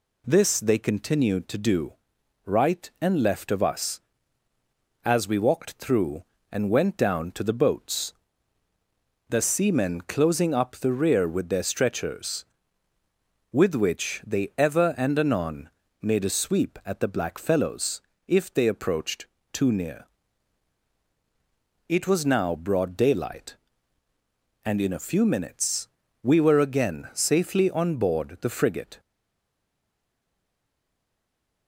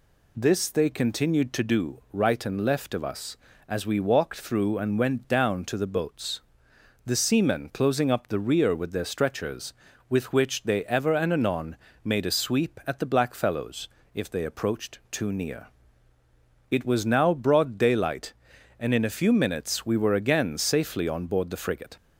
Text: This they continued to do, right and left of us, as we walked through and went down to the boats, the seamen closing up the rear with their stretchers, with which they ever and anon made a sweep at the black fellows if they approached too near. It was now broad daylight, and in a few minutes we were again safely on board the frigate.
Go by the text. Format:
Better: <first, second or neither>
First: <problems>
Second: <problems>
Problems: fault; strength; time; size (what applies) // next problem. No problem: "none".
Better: second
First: pauses between "anon" and "made"; slight; at 15.7 s; 0.32 s long // pauses between "fellows" and "if"; slight; at 18.0 s; 0.26 s long // pauses between "approached" and "too"; slight; at 19.2 s; 0.26 s long // pauses between "minutes" and "we"; slight; at 25.8 s; 0.34 s long // stays silent after the last word; strong; from 29.0 s on; 2.6 s long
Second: pauses between "anon" and "made"; slight; at 11.7 s; 0.28 s long // pauses between "fellows" and "if"; slight; at 13.8 s; 0.26 s long